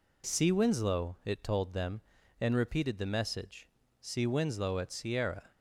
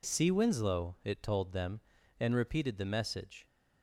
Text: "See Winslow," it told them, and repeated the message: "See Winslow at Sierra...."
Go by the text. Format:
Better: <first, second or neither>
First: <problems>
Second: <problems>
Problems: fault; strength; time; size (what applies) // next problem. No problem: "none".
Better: first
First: none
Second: stops before "See Winslow at Sierra"; at 3.4 s